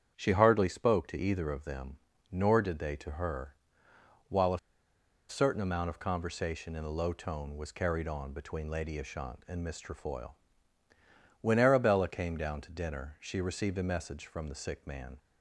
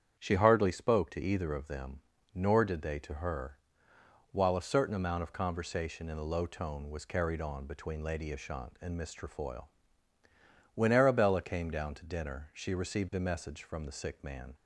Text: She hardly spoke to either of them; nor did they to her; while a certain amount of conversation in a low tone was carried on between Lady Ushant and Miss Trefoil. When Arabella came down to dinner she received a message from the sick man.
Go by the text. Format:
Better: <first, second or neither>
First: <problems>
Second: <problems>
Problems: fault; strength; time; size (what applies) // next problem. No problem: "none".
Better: second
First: starts louder than the rest; strong; until 1.1 s; 8.5 dB // pauses between "a" and "certain"; noticeable; at 4.5 s; 0.70 s long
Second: starts louder than the rest; strong; until 1.2 s; 8.5 dB